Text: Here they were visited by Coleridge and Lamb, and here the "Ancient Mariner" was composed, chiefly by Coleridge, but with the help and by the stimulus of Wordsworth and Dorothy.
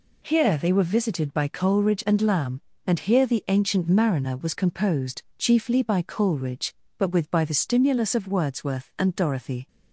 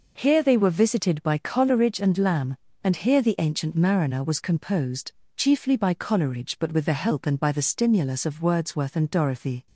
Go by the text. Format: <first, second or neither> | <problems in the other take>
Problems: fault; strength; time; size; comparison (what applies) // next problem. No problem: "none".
second | skips "the help and"; at 7.2 s